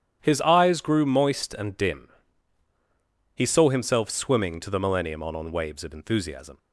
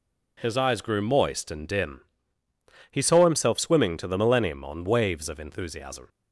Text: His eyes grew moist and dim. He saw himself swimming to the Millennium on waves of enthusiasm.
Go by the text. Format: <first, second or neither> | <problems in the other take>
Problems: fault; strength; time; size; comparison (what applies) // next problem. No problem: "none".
second | starts louder than the rest; strong; until 1.2 s; 10 dB // says "on" twice; at 5.3 s